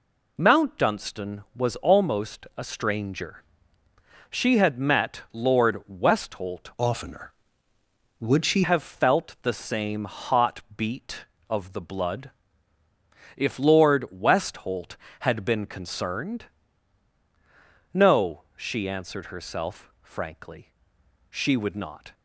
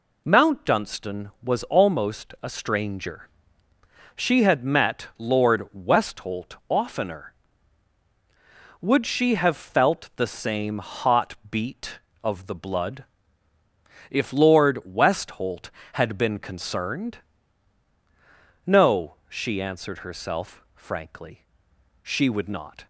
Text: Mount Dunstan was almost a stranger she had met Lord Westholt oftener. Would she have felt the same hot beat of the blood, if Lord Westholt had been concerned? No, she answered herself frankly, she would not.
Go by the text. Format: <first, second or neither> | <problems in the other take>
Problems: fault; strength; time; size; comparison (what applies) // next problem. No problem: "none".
second | pauses between "stranger" and "she"; noticeable; at 3.4 s; 0.88 s long; noticeable in the second // changes voice from "oftener" to "she"; from 6.7 to 8.6 s; 1.9 s long // pauses between "hot" and "beat"; slight; at 10.6 s; 0.16 s long; slight in the second